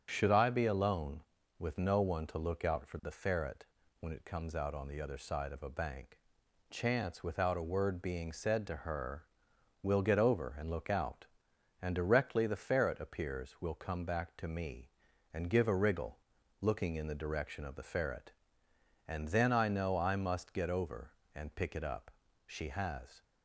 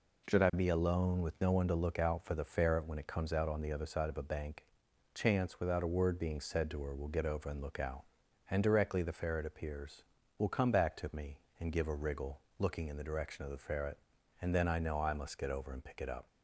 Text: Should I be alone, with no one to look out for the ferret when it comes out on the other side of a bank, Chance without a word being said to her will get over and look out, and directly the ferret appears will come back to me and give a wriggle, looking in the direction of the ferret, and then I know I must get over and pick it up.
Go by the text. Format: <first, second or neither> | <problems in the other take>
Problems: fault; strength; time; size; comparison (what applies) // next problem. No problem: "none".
second | starts louder than the rest; strong; until 1.1 s; 7.5 dB // pauses between "ferret" and "when"; slight; at 3.6 s; 0.34 s long // goes on to say "She has"; noticeable; from 22.4 s on; 0.78 s long